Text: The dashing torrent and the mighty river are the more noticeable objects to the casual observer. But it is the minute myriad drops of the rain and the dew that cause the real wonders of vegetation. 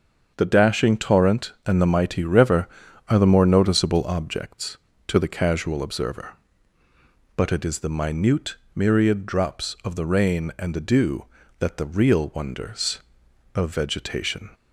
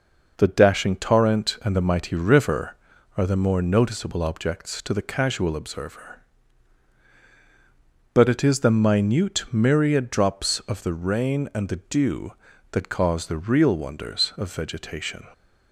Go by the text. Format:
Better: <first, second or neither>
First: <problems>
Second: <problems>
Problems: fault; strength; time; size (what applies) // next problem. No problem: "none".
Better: second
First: starts louder than the rest; until 1.3 s; 7 dB // pauses between "minute" and "myriad"; slight; at 8.5 s; 0.22 s long // skips "cause"; at 11.7 s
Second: none